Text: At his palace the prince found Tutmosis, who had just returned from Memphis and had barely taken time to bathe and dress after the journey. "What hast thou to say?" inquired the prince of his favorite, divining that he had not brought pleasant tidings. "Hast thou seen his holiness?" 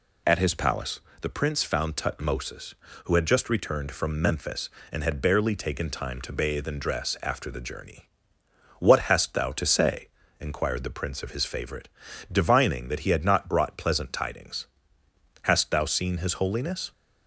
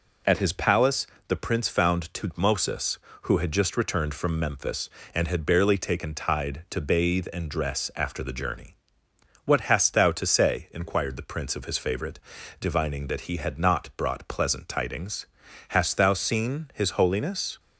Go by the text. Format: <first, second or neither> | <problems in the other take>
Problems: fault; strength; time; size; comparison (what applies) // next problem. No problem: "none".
first | pauses between "palace" and "the"; slight; at 1.0 s; 0.22 s long; slight in the first // says "tide" for "time"; at 6.1 s